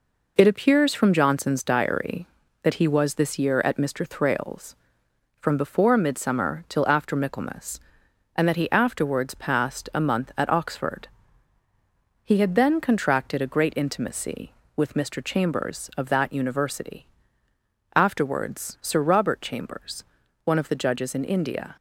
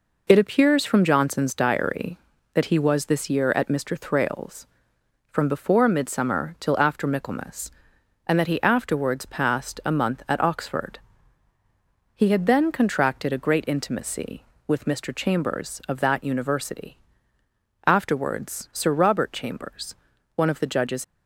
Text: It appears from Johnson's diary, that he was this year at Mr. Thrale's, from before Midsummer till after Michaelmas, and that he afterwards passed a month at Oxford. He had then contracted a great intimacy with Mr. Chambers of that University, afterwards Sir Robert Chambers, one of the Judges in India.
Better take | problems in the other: first | stops before "in India"; at 21.0 s

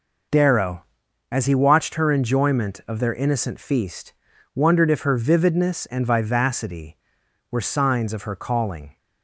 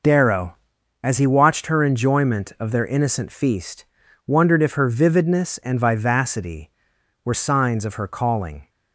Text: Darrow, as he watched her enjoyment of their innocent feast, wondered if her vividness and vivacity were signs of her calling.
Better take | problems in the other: neither | none

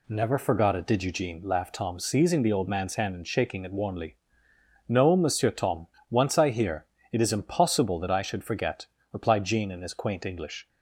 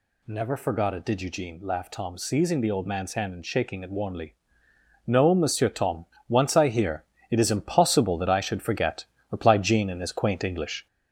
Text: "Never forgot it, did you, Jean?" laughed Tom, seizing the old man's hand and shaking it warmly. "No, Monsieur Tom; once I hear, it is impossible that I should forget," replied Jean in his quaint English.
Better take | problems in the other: first | gets louder; noticeable; throughout; 4.5 dB

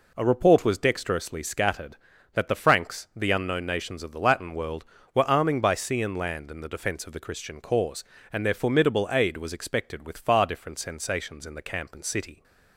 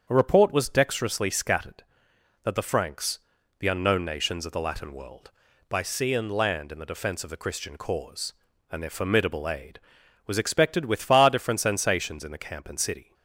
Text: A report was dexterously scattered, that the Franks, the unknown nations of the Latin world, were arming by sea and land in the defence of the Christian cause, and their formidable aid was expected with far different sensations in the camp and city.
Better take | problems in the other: first | starts louder than the rest; strong; until 1.1 s; 7.5 dB // skips "were arming"; at 5.5 s

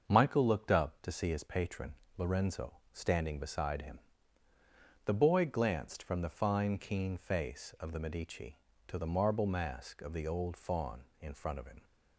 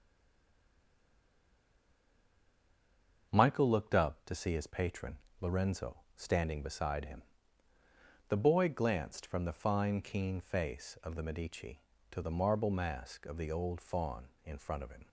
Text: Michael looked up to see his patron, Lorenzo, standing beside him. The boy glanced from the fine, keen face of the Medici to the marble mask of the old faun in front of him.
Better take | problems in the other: first | stays silent before the first word; strong; until 3.3 s; 3.3 s long // starts louder than the rest; until 4.3 s; 6.5 dB; also in the first

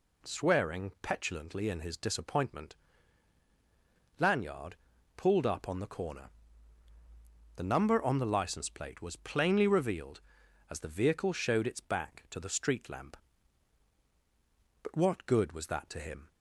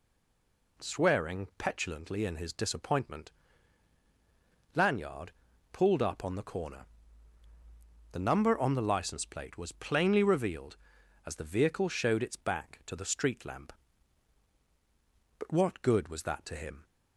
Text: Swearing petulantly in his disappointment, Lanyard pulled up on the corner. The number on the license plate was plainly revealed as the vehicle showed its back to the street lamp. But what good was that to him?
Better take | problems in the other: first | stays silent before the first word; slight; until 0.7 s; 0.7 s long // pauses between "Lanyard" and "pulled"; at 5.3 s; 0.42 s long; also in the first

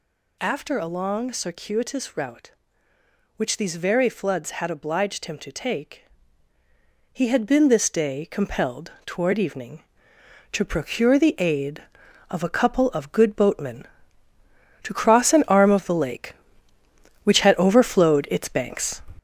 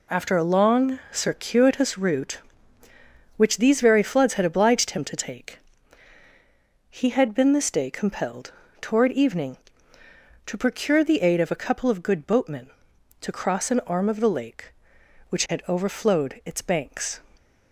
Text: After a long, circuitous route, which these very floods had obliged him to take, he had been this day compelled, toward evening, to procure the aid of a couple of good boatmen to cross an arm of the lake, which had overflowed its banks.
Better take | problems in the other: second | gets louder; noticeable; throughout; 5.5 dB

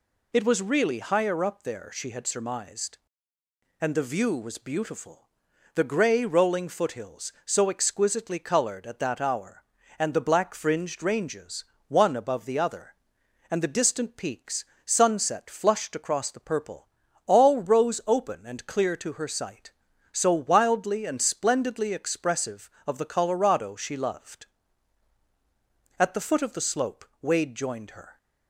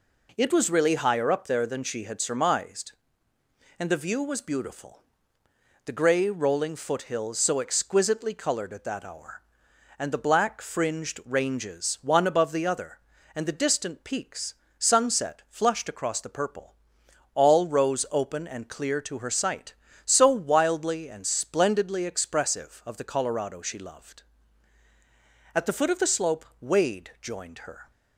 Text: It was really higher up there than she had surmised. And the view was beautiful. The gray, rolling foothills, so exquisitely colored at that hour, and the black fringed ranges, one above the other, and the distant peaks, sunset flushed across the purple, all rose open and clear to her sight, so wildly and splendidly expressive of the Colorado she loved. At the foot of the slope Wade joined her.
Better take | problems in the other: second | skips "than"; at 1.9 s // pauses between "slope" and "Wade"; slight; at 27.0 s; 0.18 s long; slight in the second

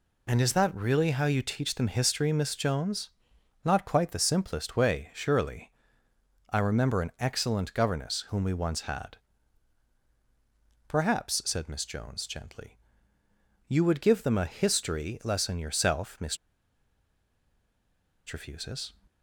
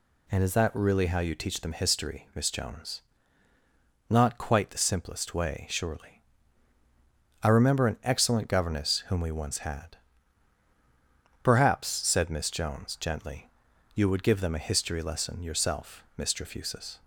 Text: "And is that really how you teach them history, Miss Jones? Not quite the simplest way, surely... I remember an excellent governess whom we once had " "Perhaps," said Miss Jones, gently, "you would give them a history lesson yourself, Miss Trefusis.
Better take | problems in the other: second | pauses between "Miss" and "Trefusis"; strong; at 16.3 s; 1.9 s long

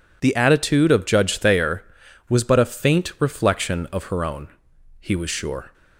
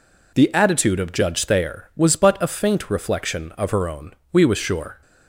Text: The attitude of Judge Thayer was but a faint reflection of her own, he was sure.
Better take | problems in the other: first | says "we" for "he"; at 4.3 s

